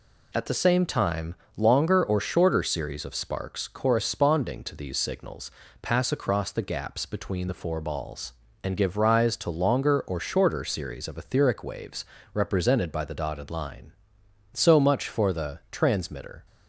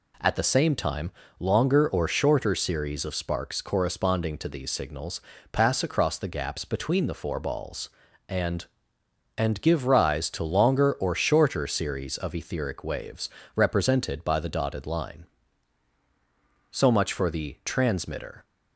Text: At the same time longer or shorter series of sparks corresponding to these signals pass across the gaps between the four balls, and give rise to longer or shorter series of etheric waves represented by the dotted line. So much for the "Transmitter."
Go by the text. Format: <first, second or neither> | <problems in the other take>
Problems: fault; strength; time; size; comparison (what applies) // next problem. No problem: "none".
first | pauses between "time" and "longer"; slight; at 1.1 s; 0.28 s long; slight in the first // pauses between "signals" and "pass"; slight; at 5.1 s; 0.32 s long; slight in the first // says "and" twice; at 9.3 s // pauses between "waves" and "represented"; slight; at 13.2 s; 0.28 s long; slight in the first